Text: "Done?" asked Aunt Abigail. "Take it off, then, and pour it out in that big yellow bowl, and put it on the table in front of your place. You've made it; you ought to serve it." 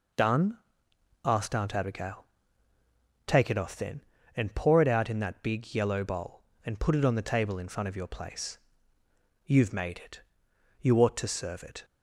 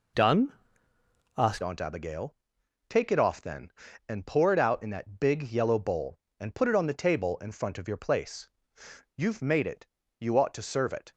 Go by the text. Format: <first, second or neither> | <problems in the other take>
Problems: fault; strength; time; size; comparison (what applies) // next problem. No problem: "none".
first | changes voice at "Aunt"; from 1.6 s on; 9.5 s long